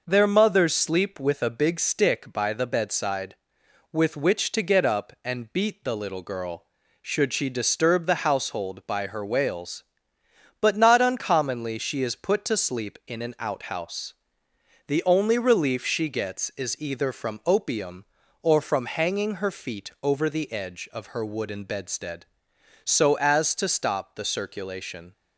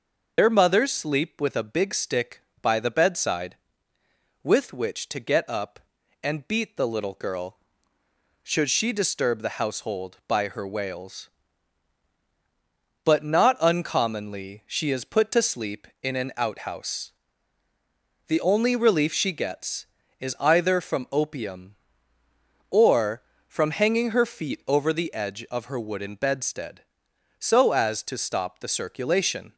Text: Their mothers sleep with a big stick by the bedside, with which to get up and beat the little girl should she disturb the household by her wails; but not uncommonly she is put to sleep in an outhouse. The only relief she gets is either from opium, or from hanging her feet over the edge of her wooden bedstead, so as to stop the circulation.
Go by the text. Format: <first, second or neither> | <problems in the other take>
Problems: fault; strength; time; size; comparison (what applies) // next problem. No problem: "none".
first | loses the start of "Their"; at 0.3 s; 75 ms